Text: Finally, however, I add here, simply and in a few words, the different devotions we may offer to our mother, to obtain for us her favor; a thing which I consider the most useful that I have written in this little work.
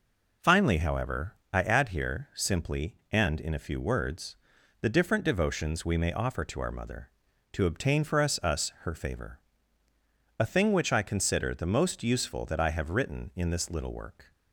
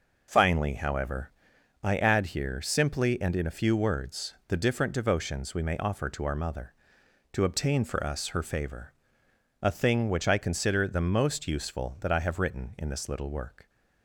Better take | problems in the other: second | says "us" twice; at 8.4 s

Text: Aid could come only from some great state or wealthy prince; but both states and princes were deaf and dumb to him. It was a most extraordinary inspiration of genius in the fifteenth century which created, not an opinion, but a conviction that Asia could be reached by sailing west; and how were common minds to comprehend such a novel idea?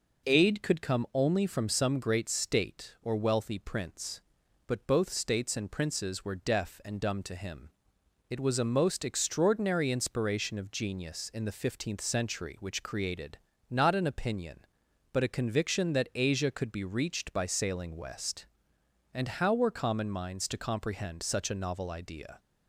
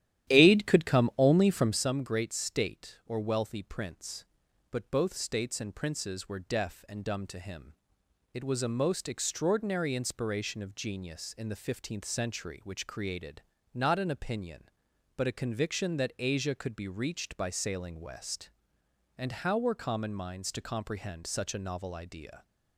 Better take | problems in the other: first | starts louder than the rest; strong; until 1.8 s; 12 dB

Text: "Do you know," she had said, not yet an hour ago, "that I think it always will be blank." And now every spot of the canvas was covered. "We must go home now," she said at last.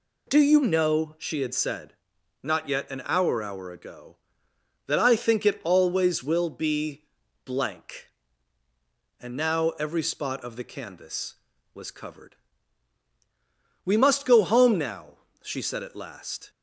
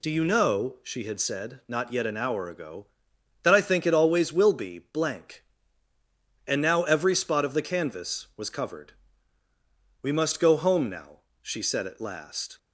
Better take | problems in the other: second | says "hour" twice; at 3.4 s // pauses between "be" and "blank"; at 7.0 s; 0.40 s long

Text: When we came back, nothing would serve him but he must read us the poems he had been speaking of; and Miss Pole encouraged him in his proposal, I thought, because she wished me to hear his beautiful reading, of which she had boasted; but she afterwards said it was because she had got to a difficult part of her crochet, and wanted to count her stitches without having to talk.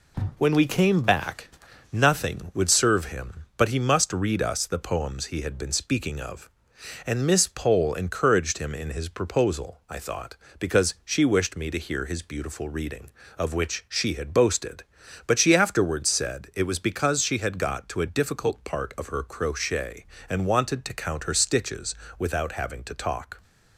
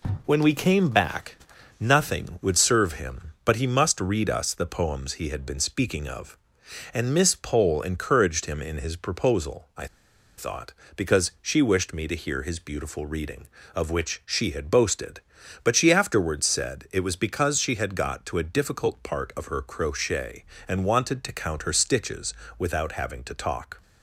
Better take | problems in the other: first | pauses between "I" and "thought"; noticeable; at 9.8 s; 0.51 s long // pauses between "stitches" and "without"; slight; at 22.3 s; 0.26 s long; slight in the first

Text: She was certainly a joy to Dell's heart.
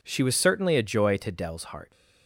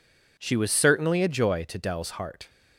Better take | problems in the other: neither | none

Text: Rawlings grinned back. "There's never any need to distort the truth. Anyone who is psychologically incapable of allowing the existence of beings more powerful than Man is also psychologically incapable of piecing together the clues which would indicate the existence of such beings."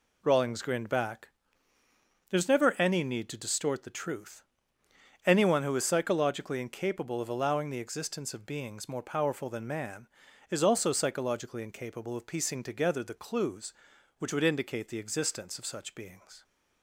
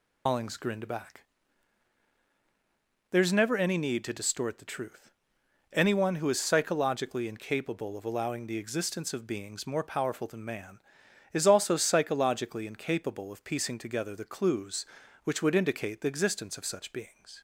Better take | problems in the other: first | loses the start of "Rawlings"; at 0.2 s; 160 ms

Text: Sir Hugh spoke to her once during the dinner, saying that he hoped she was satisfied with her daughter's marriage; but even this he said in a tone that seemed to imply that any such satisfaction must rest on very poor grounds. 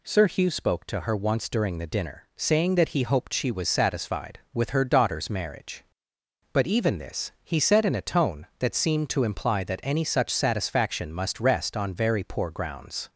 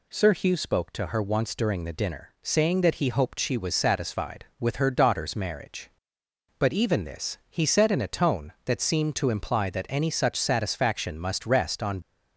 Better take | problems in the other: first | stops before "very poor grounds"; at 12.0 s

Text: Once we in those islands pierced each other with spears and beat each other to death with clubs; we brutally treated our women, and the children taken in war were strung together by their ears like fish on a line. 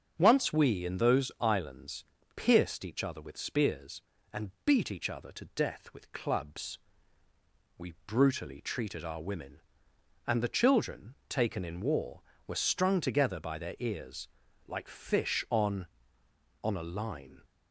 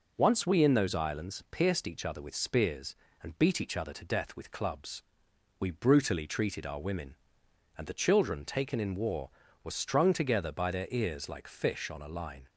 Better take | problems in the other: second | starts louder than the rest; until 1.1 s; 7 dB // pauses between "islands" and "pierced"; slight; at 2.0 s; 0.34 s long // pauses between "children" and "taken"; slight; at 11.1 s; 0.16 s long // pauses between "ears" and "like"; at 14.2 s; 0.40 s long // says "on" twice; at 16.6 s

